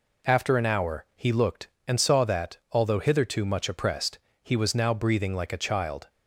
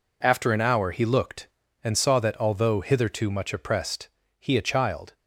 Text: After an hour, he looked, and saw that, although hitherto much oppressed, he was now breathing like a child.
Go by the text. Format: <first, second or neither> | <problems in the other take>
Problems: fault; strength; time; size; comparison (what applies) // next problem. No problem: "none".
first | skips "was now breathing like"; at 4.5 s